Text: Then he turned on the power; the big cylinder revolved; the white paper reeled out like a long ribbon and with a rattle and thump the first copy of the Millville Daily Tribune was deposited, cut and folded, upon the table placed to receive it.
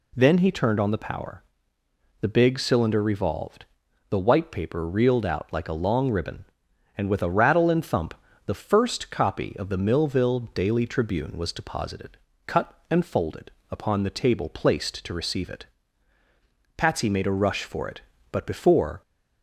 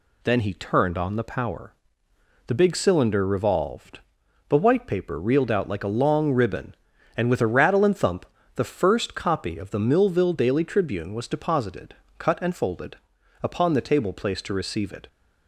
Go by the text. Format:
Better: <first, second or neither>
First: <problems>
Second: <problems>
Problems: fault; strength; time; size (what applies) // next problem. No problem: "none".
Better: second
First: pauses between "thump" and "the"; slight; at 8.1 s; 0.32 s long // goes on to say "Patsy made a rush for it but before"; strong; from 16.7 s on; 2.2 s long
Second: pauses between "thump" and "the"; slight; at 8.2 s; 0.26 s long